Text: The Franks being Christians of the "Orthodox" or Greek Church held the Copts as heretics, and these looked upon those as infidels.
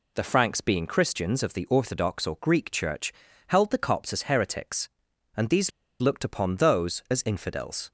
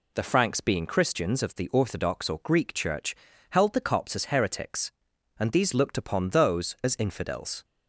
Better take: second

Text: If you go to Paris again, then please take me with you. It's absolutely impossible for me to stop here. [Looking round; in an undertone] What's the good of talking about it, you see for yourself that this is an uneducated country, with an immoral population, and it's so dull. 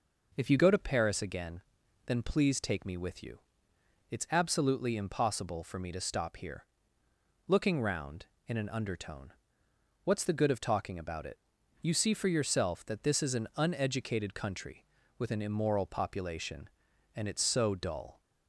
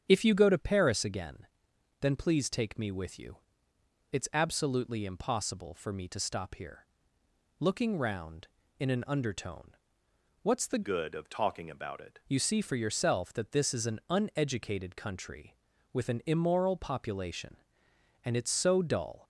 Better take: first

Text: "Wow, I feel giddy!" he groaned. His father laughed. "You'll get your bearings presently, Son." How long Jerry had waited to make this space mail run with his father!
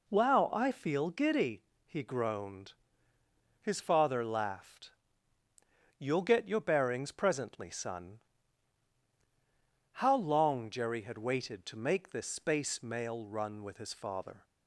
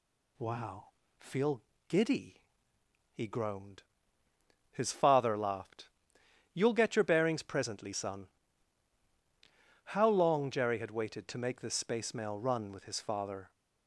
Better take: first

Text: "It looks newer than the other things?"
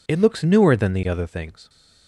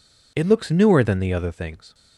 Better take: neither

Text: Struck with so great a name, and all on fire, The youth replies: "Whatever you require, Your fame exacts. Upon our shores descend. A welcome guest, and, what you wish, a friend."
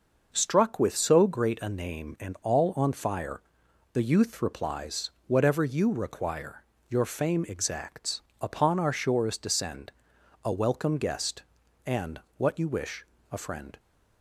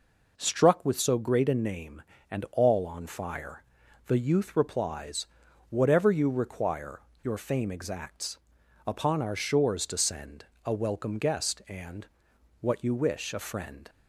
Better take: neither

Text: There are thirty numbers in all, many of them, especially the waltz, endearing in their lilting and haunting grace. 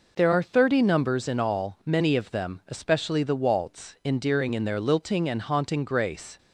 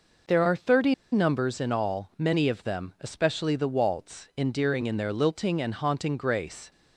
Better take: first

